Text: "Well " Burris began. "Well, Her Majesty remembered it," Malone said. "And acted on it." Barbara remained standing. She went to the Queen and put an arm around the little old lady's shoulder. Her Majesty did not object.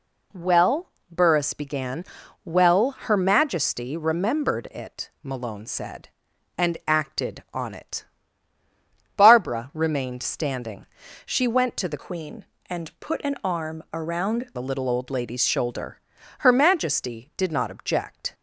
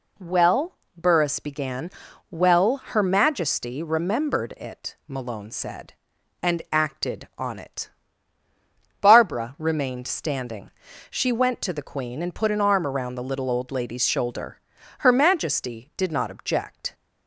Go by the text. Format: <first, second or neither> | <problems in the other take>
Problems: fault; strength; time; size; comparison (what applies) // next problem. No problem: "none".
second | changes voice from "Queen" to "around"; from 11.9 to 14.5 s; 2.6 s long